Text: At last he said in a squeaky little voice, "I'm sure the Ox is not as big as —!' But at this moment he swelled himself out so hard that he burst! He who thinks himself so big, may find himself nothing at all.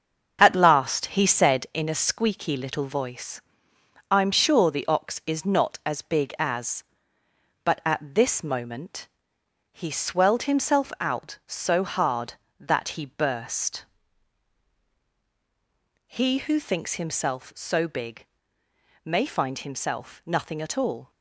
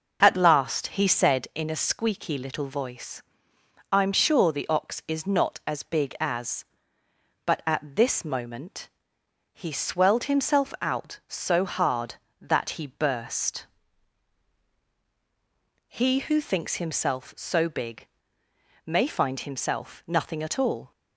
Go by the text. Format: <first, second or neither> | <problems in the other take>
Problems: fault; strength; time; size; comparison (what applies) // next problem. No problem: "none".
second | gets quieter; strong; throughout; 7 dB // starts louder than the rest; strong; until 1.5 s; 7.5 dB; also in the second // pauses between "moment" and "he"; noticeable; at 9.0 s; 0.68 s long; noticeable in the second